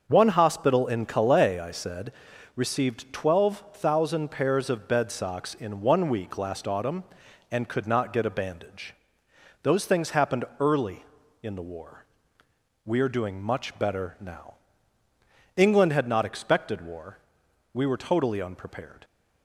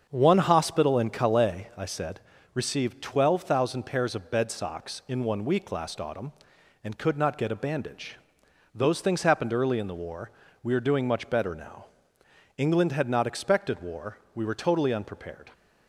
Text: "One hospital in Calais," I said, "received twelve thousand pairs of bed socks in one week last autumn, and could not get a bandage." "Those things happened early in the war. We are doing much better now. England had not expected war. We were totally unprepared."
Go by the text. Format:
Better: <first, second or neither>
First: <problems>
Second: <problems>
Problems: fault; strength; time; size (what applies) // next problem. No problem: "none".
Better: neither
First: starts louder than the rest; until 1.0 s; 6.5 dB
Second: starts louder than the rest; until 1.1 s; 7 dB